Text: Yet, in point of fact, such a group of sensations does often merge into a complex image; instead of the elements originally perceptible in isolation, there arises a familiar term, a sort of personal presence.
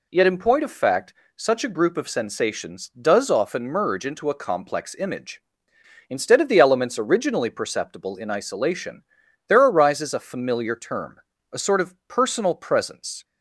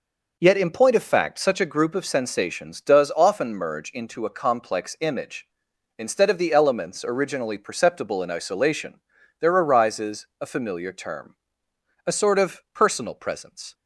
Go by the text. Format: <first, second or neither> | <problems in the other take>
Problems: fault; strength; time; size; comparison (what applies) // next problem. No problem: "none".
neither | none